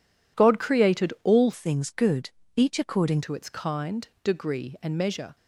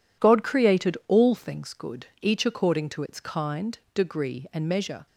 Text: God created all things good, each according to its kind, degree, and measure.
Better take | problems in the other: second | changes voice from "things" to "according"; from 1.5 to 3.2 s; 1.7 s long

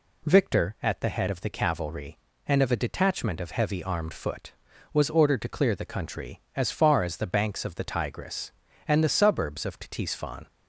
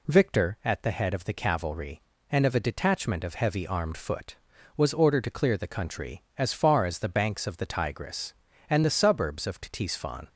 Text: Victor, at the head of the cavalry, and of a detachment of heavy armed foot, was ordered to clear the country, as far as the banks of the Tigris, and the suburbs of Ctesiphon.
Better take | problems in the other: neither | none

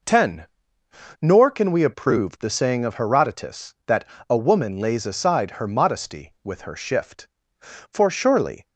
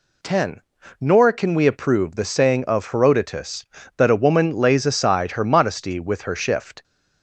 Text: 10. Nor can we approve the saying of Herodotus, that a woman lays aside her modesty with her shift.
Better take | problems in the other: second | pauses between "that" and "a"; slight; at 4.0 s; 0.26 s long // goes on to say "For surely"; noticeable; from 7.6 s on; 1.0 s long

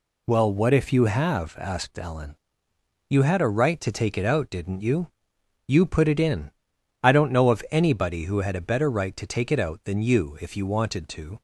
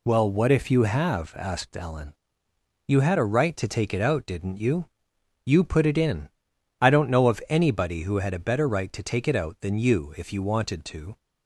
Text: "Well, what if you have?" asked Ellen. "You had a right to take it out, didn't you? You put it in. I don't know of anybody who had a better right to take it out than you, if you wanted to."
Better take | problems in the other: neither | none

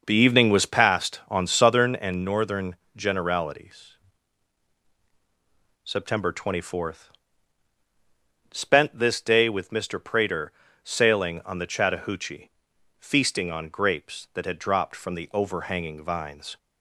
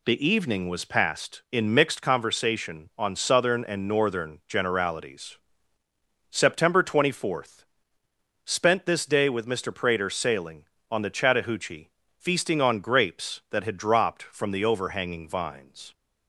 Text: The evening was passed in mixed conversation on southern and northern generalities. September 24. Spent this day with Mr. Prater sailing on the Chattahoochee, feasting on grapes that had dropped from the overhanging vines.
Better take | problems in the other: second | skips "in mixed conversation"; at 1.2 s // pauses between "northern" and "generalities"; slight; at 2.7 s; 0.22 s long // pauses between "Prater" and "sailing"; slight; at 10.5 s; 0.32 s long

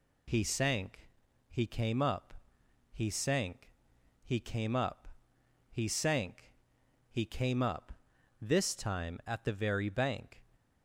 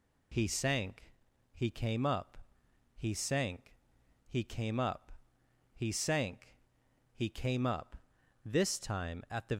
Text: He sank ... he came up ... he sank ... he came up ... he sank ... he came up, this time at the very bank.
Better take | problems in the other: first | stops before "very bank"; at 9.5 s

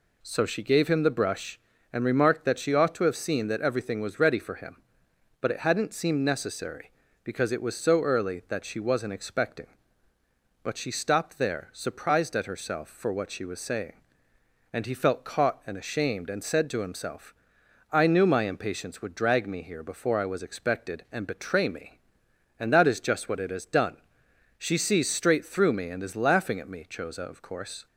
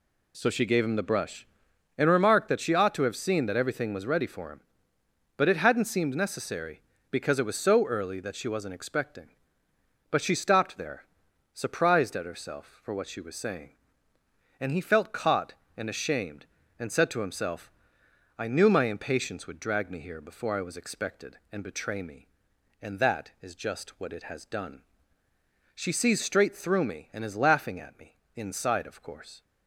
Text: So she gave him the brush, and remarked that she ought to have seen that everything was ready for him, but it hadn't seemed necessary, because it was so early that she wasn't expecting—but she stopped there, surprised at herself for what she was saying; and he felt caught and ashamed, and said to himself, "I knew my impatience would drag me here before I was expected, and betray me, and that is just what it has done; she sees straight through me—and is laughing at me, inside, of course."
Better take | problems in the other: second | says "choza" for "inside"; at 26.8 s

